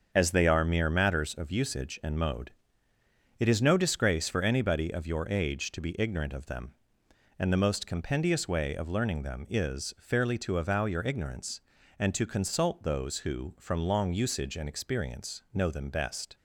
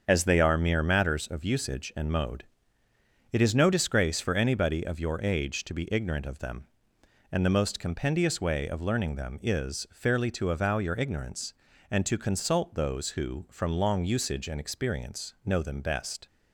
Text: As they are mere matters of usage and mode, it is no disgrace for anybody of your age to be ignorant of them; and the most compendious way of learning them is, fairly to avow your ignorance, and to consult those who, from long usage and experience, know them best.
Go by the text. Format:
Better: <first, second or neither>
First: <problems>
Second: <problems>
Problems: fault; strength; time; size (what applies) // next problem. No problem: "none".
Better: neither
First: starts louder than the rest; until 1.1 s; 6.5 dB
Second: starts louder than the rest; until 1.0 s; 7 dB